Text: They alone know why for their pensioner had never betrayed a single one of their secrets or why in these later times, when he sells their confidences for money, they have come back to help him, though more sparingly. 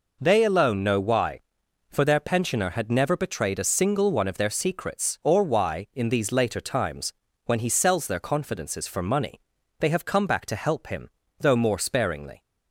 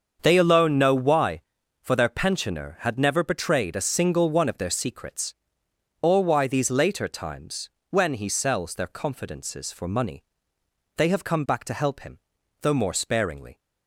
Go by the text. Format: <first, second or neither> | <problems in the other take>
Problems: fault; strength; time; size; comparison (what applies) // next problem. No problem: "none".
first | starts louder than the rest; until 1.2 s; 6.5 dB // skips "in"; at 6.4 s